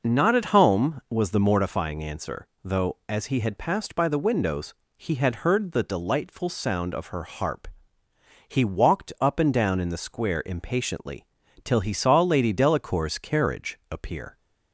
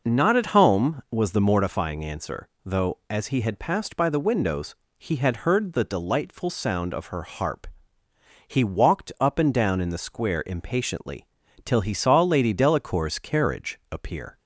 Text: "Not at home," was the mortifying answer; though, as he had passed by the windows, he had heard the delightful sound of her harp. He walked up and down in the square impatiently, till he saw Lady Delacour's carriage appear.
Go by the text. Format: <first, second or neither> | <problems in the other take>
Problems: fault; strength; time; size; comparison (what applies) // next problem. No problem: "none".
neither | none